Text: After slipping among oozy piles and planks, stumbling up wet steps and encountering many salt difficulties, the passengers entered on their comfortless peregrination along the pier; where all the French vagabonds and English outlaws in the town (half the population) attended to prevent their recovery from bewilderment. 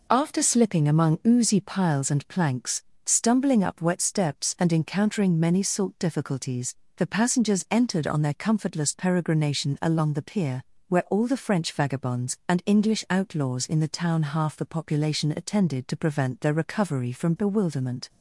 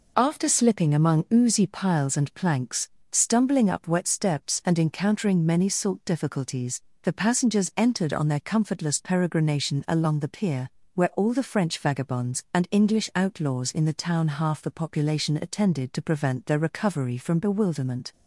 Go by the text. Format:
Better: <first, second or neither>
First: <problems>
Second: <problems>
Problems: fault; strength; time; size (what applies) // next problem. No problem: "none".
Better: neither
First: none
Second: none